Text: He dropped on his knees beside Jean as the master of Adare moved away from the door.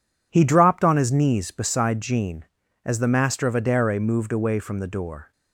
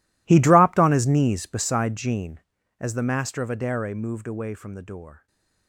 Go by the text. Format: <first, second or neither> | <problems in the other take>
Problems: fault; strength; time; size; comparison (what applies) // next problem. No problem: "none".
first | gets quieter; strong; throughout; 20 dB // stays silent after the last word; slight; from 5.1 s on; 0.5 s long